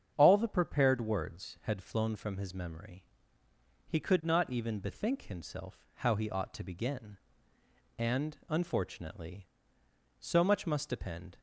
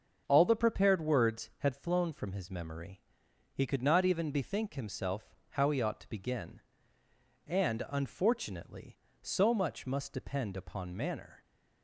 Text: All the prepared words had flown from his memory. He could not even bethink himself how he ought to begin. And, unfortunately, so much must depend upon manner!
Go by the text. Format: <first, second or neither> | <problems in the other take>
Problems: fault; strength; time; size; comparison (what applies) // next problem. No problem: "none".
second | starts louder than the rest; strong; until 1.1 s; 8 dB; also in the second // stops before "upon manner"; at 11.3 s